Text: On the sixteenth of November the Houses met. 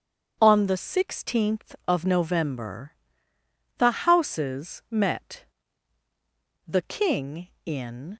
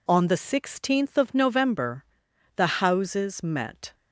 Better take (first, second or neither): second